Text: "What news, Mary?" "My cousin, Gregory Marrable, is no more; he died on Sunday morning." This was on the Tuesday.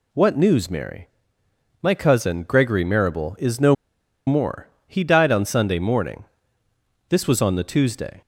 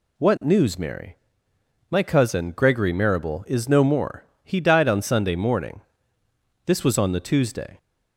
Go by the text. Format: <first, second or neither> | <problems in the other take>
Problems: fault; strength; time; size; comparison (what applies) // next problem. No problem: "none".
second | pauses between "no" and "more"; noticeable; at 3.7 s; 0.54 s long